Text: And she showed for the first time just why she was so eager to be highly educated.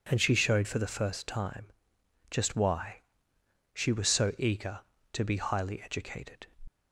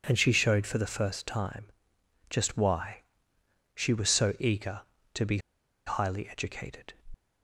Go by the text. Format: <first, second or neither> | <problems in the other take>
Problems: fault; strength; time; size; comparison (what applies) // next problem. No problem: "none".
first | pauses between "time" and "just"; noticeable; at 1.6 s; 0.64 s long; noticeable in the first // pauses between "why" and "she"; noticeable; at 3.0 s; 0.72 s long; noticeable in the first // pauses between "be" and "highly"; noticeable; at 5.3 s; 0.47 s long